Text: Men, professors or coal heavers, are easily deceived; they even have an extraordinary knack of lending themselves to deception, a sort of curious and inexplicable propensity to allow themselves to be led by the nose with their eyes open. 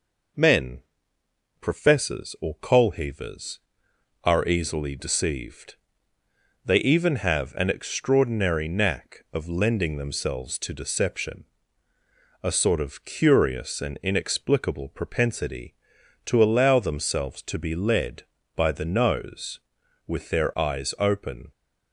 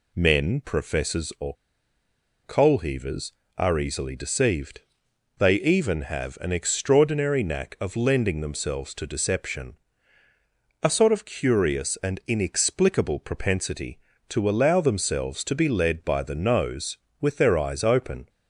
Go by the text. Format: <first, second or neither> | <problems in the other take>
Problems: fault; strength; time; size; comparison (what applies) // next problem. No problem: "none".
first | pauses between "or" and "coal"; noticeable; at 1.5 s; 0.89 s long